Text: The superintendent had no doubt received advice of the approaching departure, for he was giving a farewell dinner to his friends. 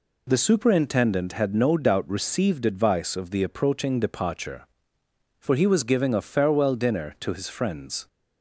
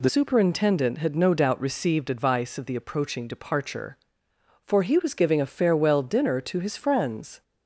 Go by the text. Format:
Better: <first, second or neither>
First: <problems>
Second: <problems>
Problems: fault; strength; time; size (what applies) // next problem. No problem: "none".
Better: first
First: none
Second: changes voice at "superintendent"; from 0.0 s on; 7.4 s long